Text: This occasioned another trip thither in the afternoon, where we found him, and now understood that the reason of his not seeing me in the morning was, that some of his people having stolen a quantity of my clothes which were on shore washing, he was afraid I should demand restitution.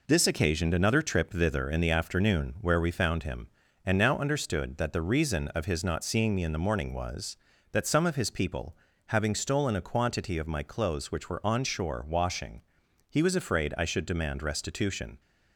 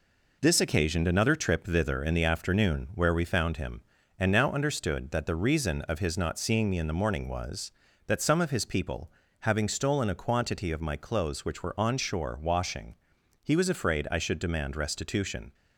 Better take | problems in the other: neither | pauses between "people" and "having"; slight; the same in both

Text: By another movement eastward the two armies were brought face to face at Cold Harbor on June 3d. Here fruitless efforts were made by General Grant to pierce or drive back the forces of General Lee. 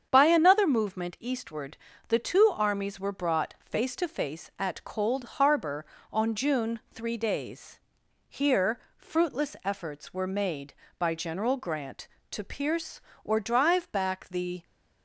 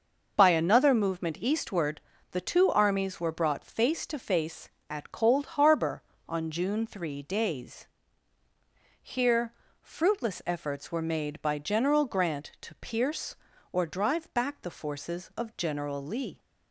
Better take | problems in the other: second | starts louder than the rest; strong; until 1.1 s; 7.5 dB // pauses between "eastward" and "the"; slight; at 1.7 s; 0.32 s long; slight in the second // pauses between "Here" and "fruitless"; slight; at 8.7 s; 0.18 s long; slight in the second // stops before "forces of General Lee"; at 14.6 s

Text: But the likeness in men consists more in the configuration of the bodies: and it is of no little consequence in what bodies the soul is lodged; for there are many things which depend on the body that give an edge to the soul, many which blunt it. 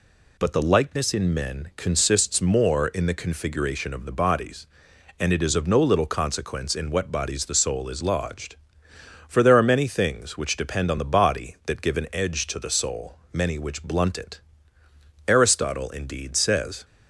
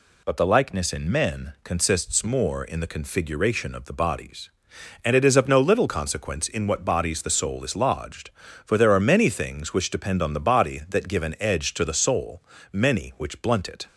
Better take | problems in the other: second | goes on to say "Aristotle indeed says"; from 15.2 s on; 1.5 s long

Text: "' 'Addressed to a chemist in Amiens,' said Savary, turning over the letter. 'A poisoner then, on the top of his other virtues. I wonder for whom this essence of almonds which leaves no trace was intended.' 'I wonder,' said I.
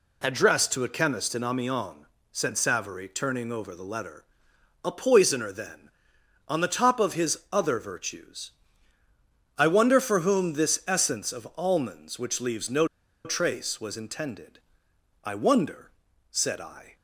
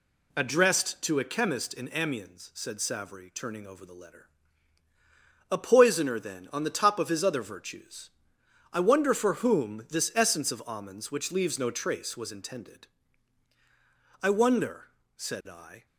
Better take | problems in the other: second | pauses between "no" and "trace"; at 12.8 s; 0.38 s long

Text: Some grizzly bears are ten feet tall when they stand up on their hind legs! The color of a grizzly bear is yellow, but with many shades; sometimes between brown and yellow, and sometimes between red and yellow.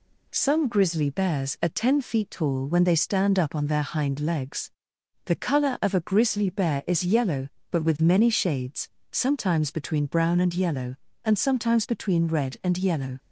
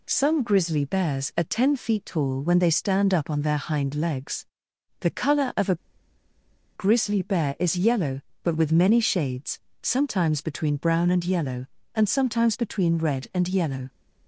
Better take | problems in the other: first | pauses between "a" and "grizzly"; at 5.7 s; 0.98 s long

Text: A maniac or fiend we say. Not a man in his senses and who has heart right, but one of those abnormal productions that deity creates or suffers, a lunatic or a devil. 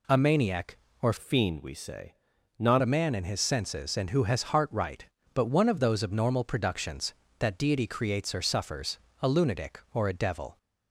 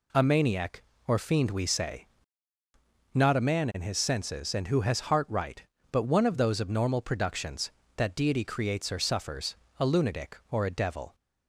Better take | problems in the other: second | changes voice from "fiend" to "Not"; from 1.1 to 2.8 s; 1.7 s long

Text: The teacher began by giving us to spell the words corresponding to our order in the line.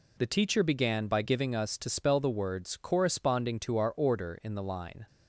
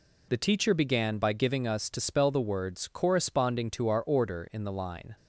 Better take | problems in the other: neither | none

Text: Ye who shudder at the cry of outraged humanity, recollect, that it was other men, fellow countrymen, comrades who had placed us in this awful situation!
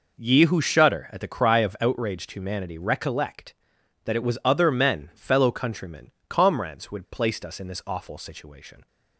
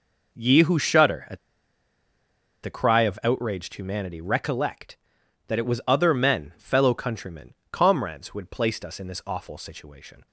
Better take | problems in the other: first | pauses between "at" and "the"; strong; at 1.3 s; 1.2 s long

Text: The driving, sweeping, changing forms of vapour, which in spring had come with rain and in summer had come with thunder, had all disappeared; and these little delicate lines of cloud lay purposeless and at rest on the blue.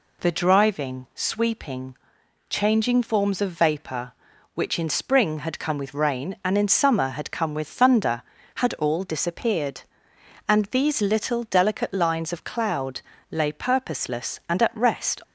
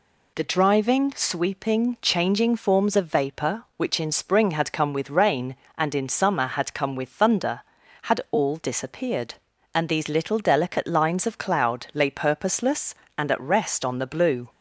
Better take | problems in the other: second | pauses between "cloud" and "lay"; slight; at 12.9 s; 0.30 s long // stops before "on the blue"; at 15.2 s

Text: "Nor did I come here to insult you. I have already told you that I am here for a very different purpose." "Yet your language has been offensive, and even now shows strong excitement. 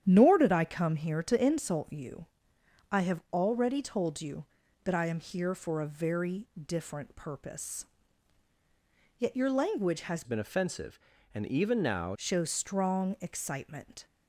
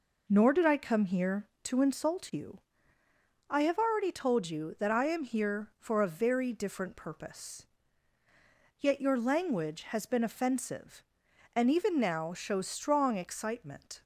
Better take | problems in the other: second | starts louder than the rest; strong; until 1.0 s; 9.5 dB // pauses between "very" and "different"; slight; at 6.4 s; 0.16 s long // changes voice from "been" to "now"; from 10.2 to 12.1 s; 1.9 s long

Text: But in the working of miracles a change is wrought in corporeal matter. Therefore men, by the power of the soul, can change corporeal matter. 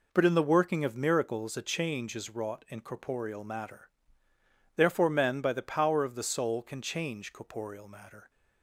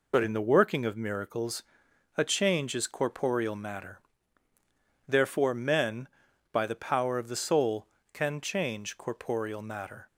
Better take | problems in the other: first | pauses between "miracles" and "a"; noticeable; at 1.6 s; 0.52 s long // skips "wrought in"; at 2.8 s

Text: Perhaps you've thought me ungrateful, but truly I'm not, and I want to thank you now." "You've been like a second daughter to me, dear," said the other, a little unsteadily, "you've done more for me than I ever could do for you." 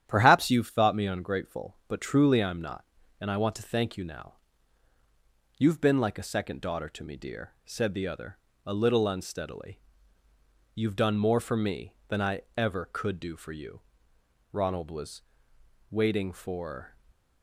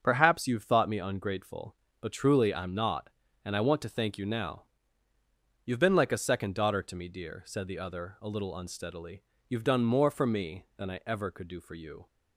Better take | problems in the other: second | starts louder than the rest; strong; until 1.0 s; 10 dB; also in the second // pauses between "I" and "ever"; slight; at 12.4 s; 0.16 s long // goes on to say "Ronald was waiting for"; strong; from 14.5 s on; 2.4 s long

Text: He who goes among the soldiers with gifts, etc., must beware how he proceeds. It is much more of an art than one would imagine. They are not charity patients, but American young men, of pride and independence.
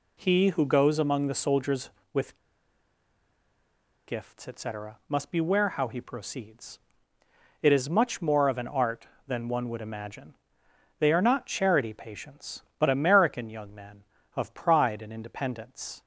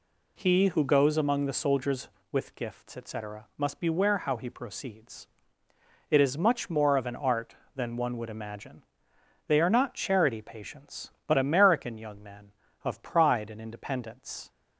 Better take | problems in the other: second | pauses between "with" and "gifts"; strong; at 2.3 s; 1.7 s long

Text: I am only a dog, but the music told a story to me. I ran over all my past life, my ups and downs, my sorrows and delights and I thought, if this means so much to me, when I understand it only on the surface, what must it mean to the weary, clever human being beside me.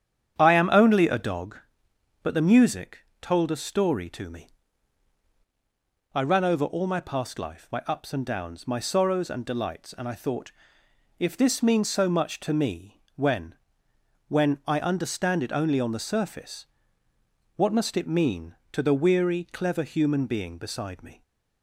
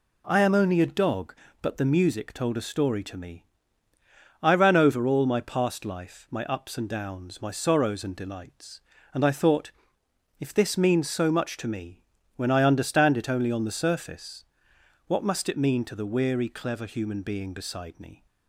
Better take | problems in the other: second | starts louder than the rest; strong; until 1.4 s; 9 dB // pauses between "music" and "told"; slight; at 2.9 s; 0.24 s long // says "when" twice; at 14.2 s

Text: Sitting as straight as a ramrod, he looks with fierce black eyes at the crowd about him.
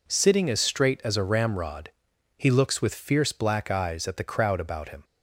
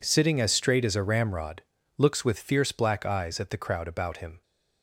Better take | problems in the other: first | skips "he"; at 1.7 s

